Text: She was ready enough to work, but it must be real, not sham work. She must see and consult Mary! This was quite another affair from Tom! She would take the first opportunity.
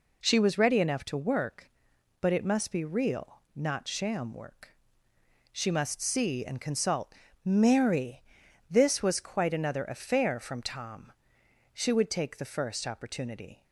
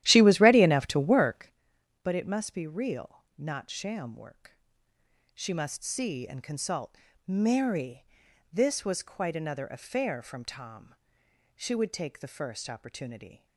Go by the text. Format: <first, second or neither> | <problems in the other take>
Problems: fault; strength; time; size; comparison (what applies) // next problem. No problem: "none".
first | starts louder than the rest; strong; until 1.6 s; 13 dB // pauses between "consult" and "Mary"; slight; at 6.9 s; 0.32 s long; slight in the first